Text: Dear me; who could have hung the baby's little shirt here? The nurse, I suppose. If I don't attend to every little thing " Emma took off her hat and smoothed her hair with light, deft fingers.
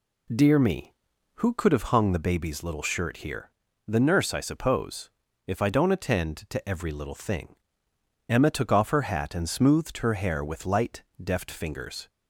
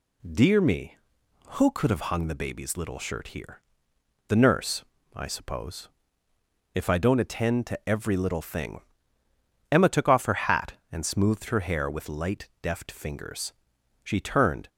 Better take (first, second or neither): first